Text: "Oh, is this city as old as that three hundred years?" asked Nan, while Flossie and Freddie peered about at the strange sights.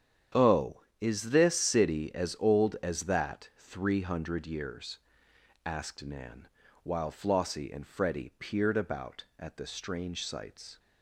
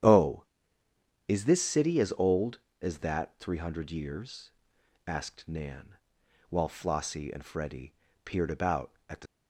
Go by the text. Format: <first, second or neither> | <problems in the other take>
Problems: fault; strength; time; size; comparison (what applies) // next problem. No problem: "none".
first | starts louder than the rest; strong; until 1.9 s; 10 dB; strong in the first // pauses between "Freddie" and "peered"; slight; at 7.9 s; 0.32 s long // stops before "strange sights"; at 9.2 s